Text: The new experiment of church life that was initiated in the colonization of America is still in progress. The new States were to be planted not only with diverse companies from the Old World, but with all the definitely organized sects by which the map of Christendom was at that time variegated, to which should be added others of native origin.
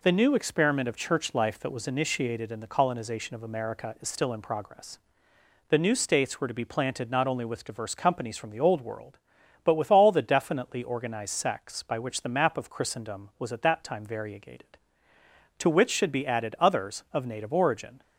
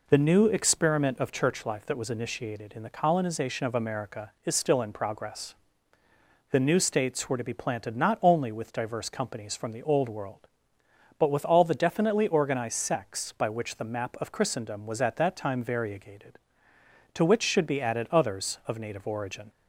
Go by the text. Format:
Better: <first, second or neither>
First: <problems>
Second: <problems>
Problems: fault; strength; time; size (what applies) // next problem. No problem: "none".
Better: neither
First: none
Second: none